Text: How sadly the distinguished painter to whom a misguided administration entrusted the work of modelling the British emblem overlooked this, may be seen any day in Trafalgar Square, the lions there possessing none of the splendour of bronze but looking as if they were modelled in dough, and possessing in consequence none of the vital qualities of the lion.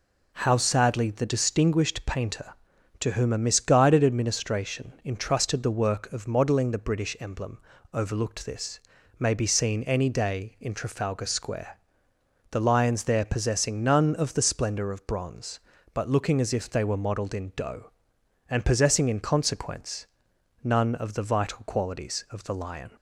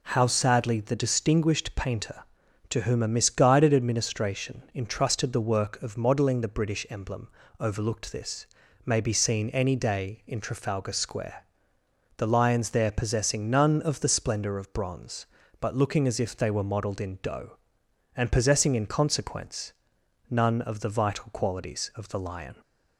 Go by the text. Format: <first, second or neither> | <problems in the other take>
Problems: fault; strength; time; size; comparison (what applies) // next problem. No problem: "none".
neither | pauses between "emblem" and "overlooked"; slight; the same in both // pauses between "consequence" and "none"; noticeable; the same in both